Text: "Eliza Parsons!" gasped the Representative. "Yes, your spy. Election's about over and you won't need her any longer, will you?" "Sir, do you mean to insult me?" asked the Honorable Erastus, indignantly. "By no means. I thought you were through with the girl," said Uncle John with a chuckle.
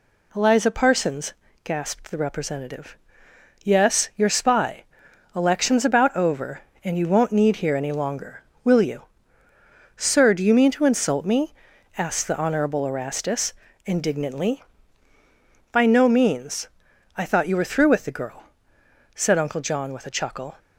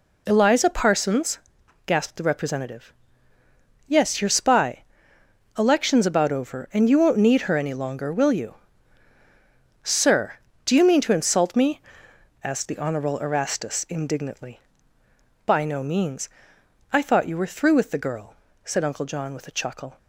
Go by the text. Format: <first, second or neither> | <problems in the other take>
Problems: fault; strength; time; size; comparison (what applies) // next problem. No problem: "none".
second | says "here" for "her"; at 7.5 s